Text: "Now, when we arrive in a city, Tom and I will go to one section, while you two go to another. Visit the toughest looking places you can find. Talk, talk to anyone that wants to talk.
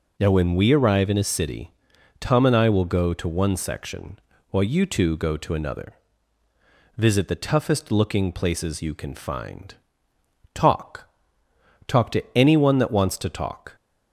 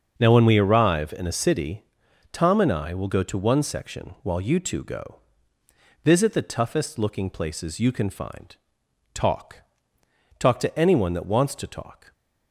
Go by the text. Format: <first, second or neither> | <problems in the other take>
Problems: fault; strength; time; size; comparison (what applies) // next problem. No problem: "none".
first | starts louder than the rest; until 1.1 s; 6.5 dB // skips "to another"; at 5.6 s